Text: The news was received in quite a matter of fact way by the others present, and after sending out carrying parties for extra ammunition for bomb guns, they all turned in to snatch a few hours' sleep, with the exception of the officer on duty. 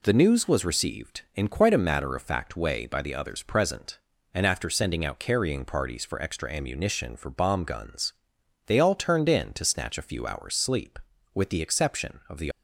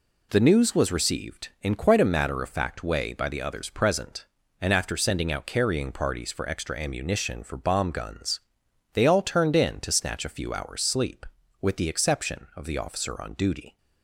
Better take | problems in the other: second | stops before "officer on duty"; at 12.5 s

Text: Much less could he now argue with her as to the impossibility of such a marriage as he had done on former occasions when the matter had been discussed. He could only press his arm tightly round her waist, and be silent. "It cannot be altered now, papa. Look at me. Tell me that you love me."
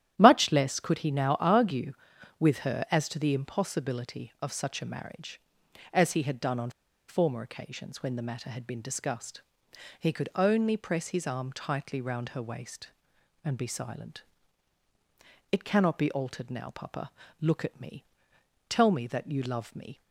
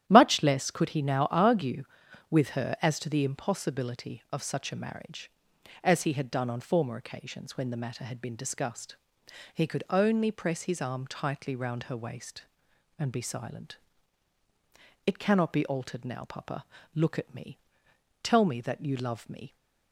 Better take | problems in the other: second | starts louder than the rest; strong; until 1.2 s; 11 dB; strong in the second // pauses between "on" and "former"; at 6.6 s; 0.38 s long

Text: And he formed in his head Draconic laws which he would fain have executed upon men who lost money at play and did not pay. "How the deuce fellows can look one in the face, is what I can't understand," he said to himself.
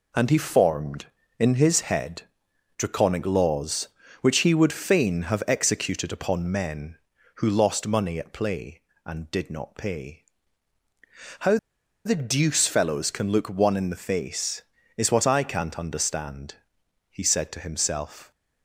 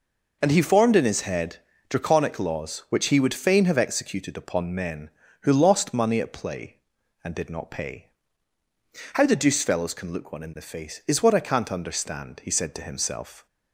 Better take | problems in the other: second | pauses between "head" and "Draconic"; noticeable; at 2.2 s; 0.54 s long; slight in the second // pauses between "How" and "the"; noticeable; at 11.5 s; 0.48 s long

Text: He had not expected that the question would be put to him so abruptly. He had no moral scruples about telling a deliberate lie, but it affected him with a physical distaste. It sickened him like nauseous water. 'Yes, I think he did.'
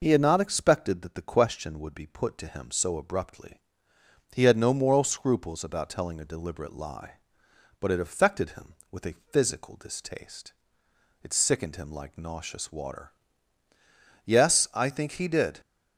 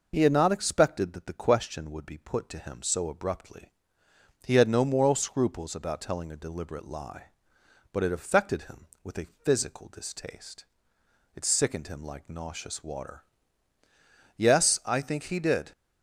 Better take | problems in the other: neither | none

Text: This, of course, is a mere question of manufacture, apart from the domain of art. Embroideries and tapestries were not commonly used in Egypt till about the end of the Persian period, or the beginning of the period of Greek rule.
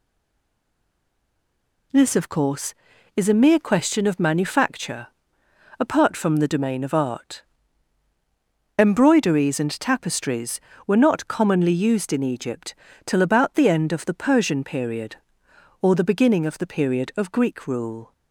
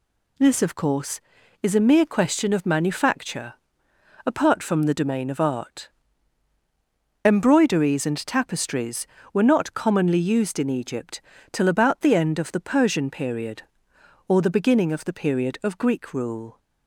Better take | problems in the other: second | stays silent before the first word; noticeable; until 1.9 s; 1.9 s long // pauses between "Egypt" and "till"; slight; at 12.7 s; 0.32 s long; slight in the second

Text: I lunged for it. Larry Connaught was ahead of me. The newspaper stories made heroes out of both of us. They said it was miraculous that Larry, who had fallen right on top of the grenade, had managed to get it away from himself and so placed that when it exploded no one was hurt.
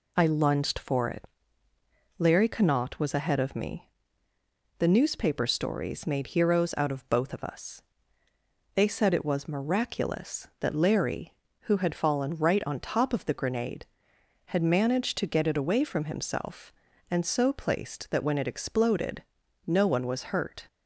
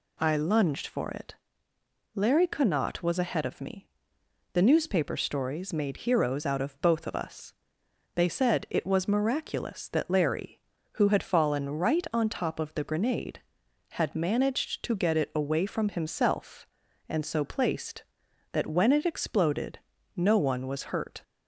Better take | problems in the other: neither | pauses between "exploded" and "no"; the same in both

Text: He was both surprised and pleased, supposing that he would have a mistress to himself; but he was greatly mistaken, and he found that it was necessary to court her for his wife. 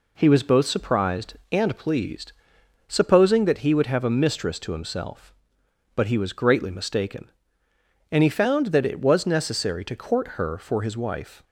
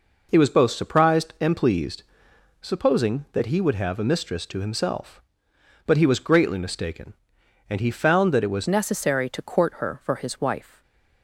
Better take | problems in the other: first | changes voice at "necessary"; from 8.6 s on; 2.2 s long // stays silent after the last word; slight; from 10.6 s on; 0.6 s long

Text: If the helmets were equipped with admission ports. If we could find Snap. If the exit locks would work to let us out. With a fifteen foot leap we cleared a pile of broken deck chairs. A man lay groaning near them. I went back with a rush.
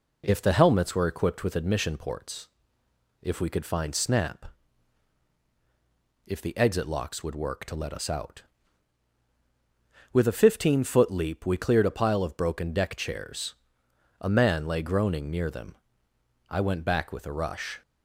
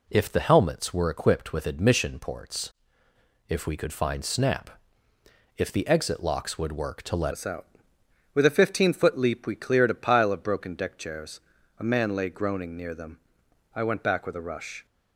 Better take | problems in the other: first | changes voice at "us"; from 7.3 s on; 7.5 s long

